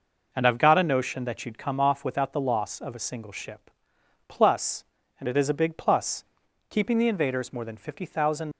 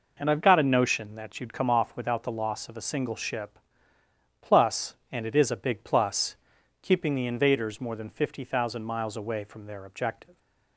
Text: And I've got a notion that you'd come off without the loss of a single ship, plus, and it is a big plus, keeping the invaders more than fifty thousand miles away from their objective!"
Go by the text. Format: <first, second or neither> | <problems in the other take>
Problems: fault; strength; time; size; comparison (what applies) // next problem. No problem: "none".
second | stops before "miles away from their objective"; at 8.5 s